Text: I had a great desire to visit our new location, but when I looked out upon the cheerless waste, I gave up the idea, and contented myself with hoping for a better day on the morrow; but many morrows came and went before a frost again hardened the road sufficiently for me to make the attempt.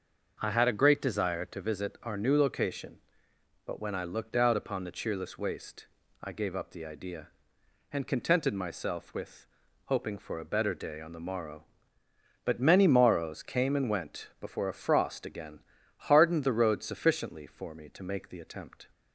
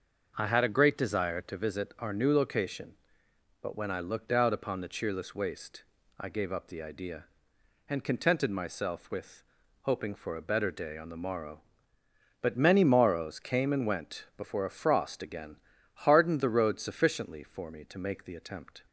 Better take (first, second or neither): neither